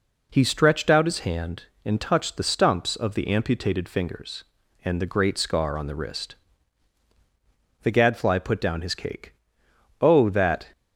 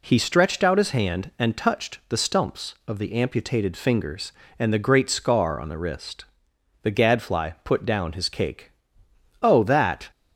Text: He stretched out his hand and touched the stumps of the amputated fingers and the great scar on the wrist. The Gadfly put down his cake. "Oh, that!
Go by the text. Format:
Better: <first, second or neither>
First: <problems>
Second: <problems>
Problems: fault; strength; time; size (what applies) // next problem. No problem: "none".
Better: neither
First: none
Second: none